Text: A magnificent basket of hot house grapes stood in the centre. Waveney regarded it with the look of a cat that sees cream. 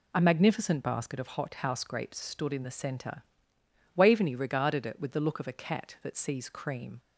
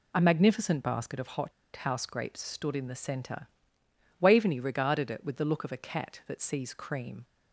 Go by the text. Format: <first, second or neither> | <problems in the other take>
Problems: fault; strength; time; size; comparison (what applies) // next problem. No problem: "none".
first | pauses between "hot" and "house"; slight; at 1.5 s; 0.24 s long